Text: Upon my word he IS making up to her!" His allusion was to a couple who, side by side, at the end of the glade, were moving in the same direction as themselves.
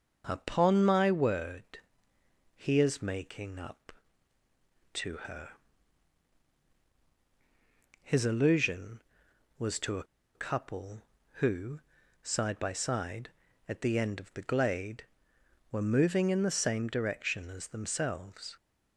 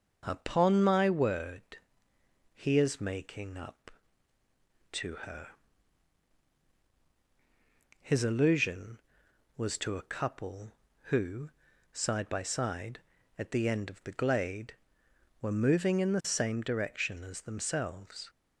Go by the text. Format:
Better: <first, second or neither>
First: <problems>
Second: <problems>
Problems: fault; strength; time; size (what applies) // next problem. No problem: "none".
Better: second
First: starts louder than the rest; until 1.2 s; 6 dB // pauses between "word" and "he"; noticeable; at 1.7 s; 0.78 s long // pauses between "a" and "couple"; slight; at 10.0 s; 0.31 s long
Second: starts louder than the rest; until 1.2 s; 6.5 dB // pauses between "word" and "he"; noticeable; at 1.7 s; 0.78 s long